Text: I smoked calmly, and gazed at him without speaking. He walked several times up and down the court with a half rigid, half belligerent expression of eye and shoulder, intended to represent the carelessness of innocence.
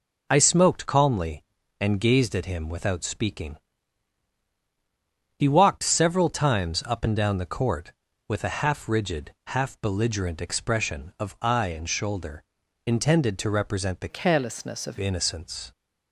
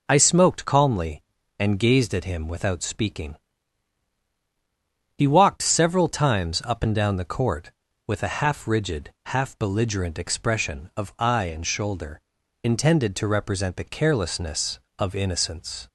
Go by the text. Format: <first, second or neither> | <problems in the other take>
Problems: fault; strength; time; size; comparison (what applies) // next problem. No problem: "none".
second | changes voice from "carelessness" to "of"; from 14.0 to 14.9 s; 0.9 s long